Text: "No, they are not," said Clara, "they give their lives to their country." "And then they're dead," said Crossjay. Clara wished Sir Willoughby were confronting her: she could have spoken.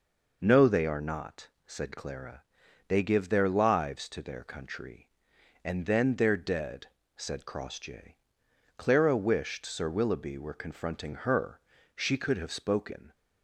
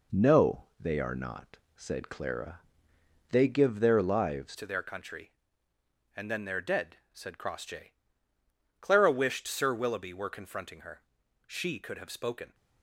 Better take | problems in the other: first | changes voice at "to"; from 4.5 s on; 8.0 s long

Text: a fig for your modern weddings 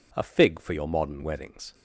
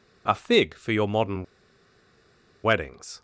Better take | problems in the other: first | pauses between "modern" and "weddings"; at 1.4 s; 1.1 s long

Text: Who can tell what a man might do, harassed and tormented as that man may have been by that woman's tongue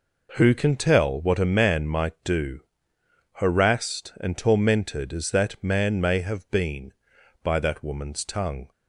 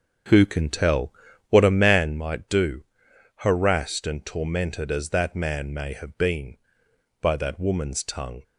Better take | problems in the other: first | starts louder than the rest; strong; until 2.2 s; 7.5 dB // pauses between "tell" and "what"; at 1.1 s; 0.38 s long

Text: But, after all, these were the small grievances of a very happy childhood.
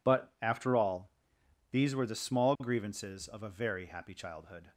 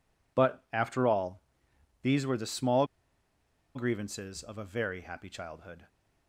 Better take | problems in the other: first | pauses between "small" and "grievances"; noticeable; at 2.8 s; 0.89 s long

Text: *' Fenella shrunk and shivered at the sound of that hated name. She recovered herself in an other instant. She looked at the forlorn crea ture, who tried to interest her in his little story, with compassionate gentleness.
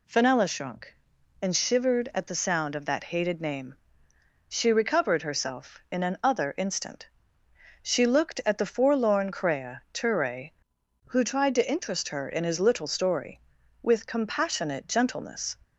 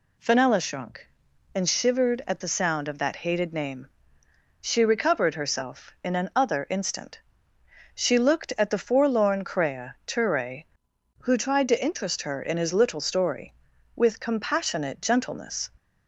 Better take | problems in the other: neither | none

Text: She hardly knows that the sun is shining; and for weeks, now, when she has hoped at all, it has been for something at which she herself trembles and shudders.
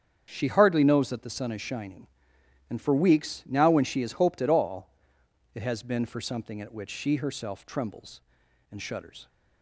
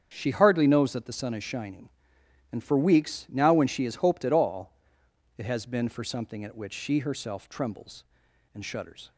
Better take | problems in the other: neither | starts louder than the rest; strong; the same in both

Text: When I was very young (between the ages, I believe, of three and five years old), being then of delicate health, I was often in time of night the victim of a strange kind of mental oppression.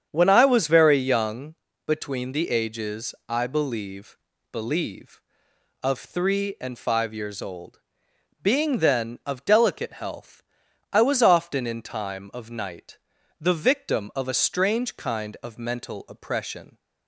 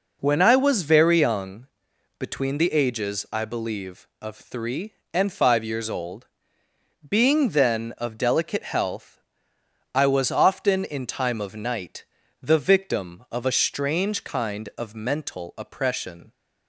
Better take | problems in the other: second | starts louder than the rest; strong; until 1.1 s; 8 dB // says "believe" twice; at 4.5 s // pauses between "night" and "the"; at 12.9 s; 0.38 s long; also in the second

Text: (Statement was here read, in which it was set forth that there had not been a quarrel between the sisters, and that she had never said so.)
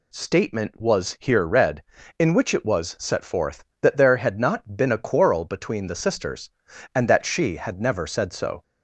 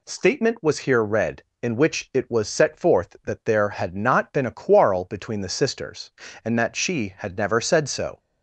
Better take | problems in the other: neither | none

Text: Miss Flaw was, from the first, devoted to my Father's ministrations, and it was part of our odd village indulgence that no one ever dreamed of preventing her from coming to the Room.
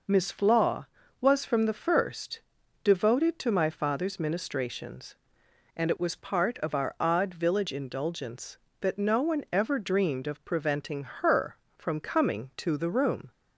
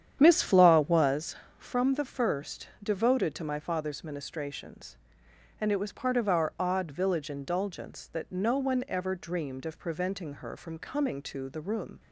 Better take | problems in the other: first | starts louder than the rest; strong; until 1.2 s; 9 dB

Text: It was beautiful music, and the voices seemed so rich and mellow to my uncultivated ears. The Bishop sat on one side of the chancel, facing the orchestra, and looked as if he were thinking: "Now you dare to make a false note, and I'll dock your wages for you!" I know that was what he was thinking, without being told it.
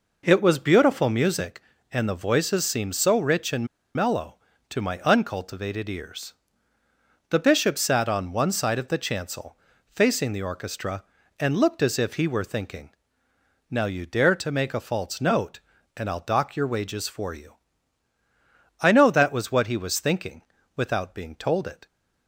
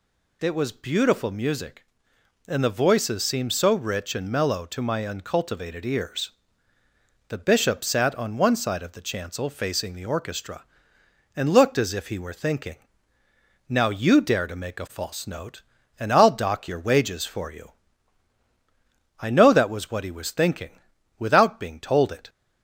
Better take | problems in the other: second | pauses between "and" and "mellow"; slight; at 3.6 s; 0.28 s long

